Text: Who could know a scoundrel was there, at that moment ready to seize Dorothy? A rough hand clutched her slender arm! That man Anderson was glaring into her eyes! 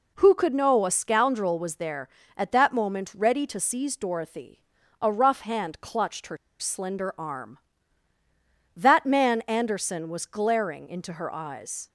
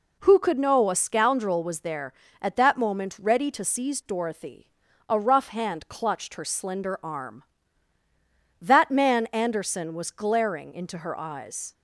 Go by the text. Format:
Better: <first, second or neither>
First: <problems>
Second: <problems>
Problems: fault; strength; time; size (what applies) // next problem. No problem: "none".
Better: second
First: pauses between "her" and "slender"; slight; at 6.3 s; 0.22 s long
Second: none